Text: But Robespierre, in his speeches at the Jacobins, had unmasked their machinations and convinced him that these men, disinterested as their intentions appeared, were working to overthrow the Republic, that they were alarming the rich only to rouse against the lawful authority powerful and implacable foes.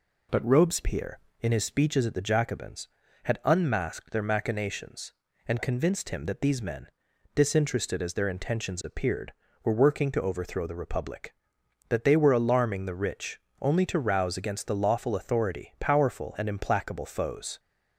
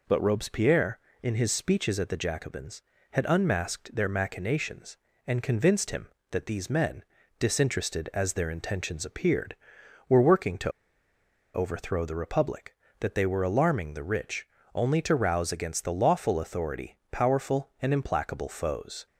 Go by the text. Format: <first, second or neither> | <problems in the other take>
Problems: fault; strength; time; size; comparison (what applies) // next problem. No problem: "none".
first | pauses between "to" and "overthrow"; noticeable; at 10.7 s; 0.83 s long // pauses between "rich" and "only"; slight; at 14.4 s; 0.28 s long; slight in the first